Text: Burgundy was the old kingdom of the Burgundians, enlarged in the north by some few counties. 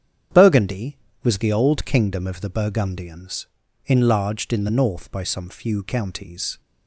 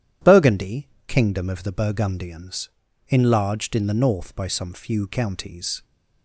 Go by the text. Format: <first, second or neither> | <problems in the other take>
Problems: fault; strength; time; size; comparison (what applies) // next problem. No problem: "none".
first | starts louder than the rest; strong; until 1.4 s; 10.5 dB; strong in the first // skips "was the old"; at 0.9 s